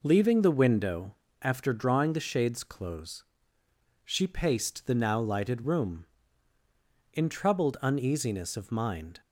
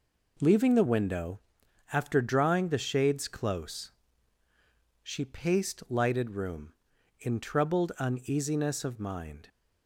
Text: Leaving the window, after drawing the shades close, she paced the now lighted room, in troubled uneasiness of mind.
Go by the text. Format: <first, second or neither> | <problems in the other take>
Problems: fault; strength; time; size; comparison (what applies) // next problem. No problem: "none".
first | skips "the now"; at 5.8 s